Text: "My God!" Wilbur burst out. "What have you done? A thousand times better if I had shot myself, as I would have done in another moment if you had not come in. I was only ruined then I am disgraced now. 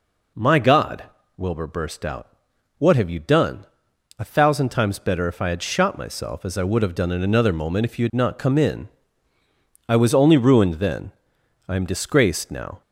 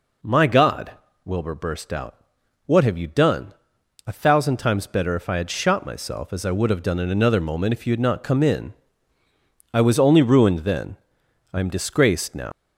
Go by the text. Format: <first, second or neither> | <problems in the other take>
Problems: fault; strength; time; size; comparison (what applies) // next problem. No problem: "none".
first | pauses between "then" and "I"; noticeable; at 10.9 s; 0.56 s long; noticeable in the first // leaves "now" unfinished; at 12.5 s; 135 ms